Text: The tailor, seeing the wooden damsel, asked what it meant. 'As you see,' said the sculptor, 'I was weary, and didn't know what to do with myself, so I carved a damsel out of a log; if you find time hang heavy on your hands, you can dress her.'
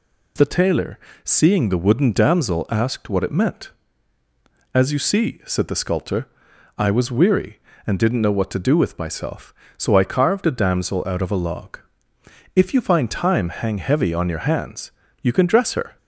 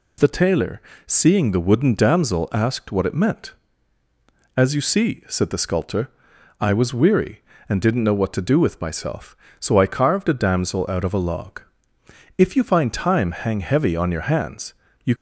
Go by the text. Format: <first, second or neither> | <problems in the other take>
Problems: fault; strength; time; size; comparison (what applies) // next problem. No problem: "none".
first | stops before "can dress her"; at 15.1 s